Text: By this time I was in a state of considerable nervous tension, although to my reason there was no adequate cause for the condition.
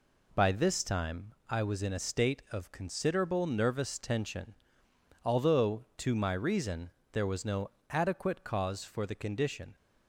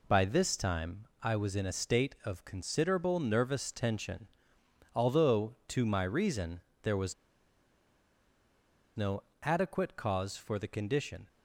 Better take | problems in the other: first | pauses between "time" and "I"; slight; at 1.0 s; 0.16 s long; slight in the first // pauses between "reason" and "there"; slight; at 6.6 s; 0.22 s long; slight in the first // pauses between "was" and "no"; strong; at 7.1 s; 1.8 s long // pauses between "no" and "adequate"; slight; at 9.2 s; 0.20 s long; slight in the first

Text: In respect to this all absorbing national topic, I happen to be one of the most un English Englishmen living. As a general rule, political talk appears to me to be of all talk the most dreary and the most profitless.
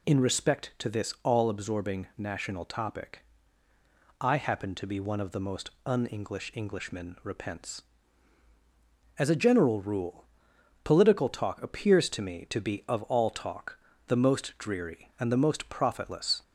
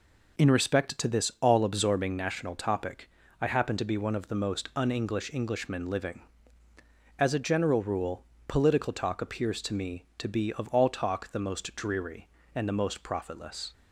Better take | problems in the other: second | pauses between "most" and "un"; slight; at 5.7 s; 0.16 s long // says "repents" for "living"; at 7.2 s // pauses between "talk" and "the"; slight; at 13.7 s; 0.30 s long

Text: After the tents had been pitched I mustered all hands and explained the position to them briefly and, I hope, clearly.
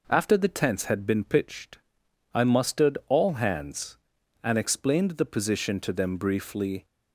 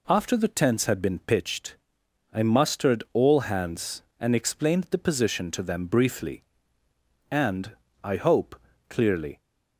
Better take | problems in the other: second | pauses between "pitched" and "I"; noticeable; at 1.7 s; 0.56 s long; noticeable in the second // stops before "and I hope clearly"; at 6.8 s

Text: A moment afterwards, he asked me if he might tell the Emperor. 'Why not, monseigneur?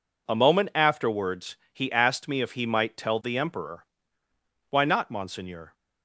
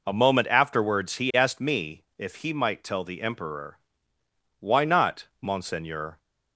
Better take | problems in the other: neither | none

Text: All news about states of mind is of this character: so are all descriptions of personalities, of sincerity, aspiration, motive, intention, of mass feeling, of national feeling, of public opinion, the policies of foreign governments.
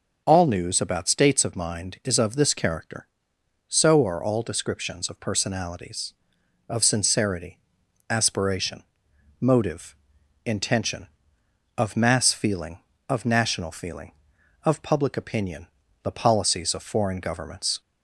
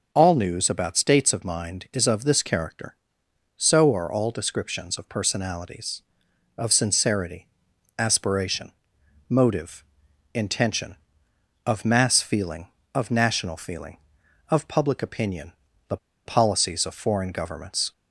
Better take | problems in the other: first | pauses between "the" and "policies"; slight; at 15.9 s; 0.27 s long

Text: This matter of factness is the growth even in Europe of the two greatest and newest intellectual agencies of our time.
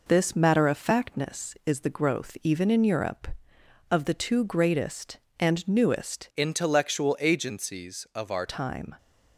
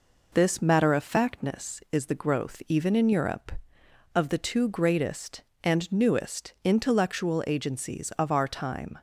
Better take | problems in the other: second | changes voice from "intellectual" to "our"; from 6.3 to 8.4 s; 2.1 s long

